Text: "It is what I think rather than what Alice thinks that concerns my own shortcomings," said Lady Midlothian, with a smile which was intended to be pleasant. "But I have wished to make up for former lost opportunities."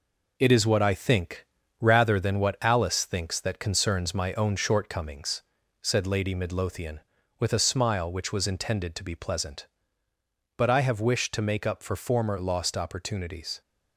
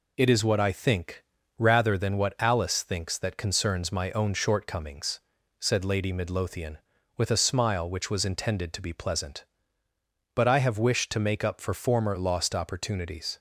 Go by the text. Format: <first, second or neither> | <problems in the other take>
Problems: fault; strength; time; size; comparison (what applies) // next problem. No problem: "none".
second | gets quieter; noticeable; throughout; 5.5 dB // pauses between "think" and "rather"; slight; at 1.4 s; 0.34 s long; slight in the second